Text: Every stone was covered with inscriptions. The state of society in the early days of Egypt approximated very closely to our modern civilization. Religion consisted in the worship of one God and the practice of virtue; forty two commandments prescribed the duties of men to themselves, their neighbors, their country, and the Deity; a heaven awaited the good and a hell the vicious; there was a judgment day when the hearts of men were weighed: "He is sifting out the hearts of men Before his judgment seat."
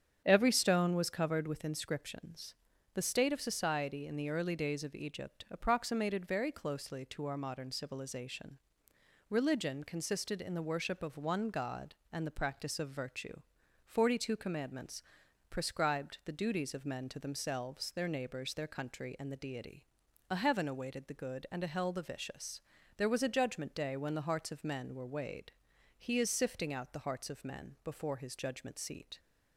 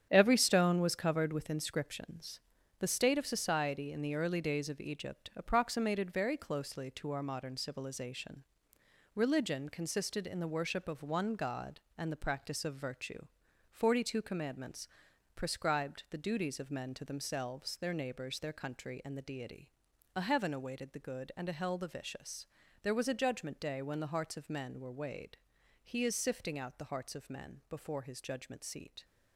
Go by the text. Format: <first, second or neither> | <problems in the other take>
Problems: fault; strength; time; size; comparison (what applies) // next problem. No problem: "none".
first | gets quieter; strong; throughout; 9 dB // starts louder than the rest; strong; until 1.1 s; 8.5 dB; strong in the first // pauses between "commandments" and "prescribed"; noticeable; at 14.8 s; 0.46 s long; noticeable in the first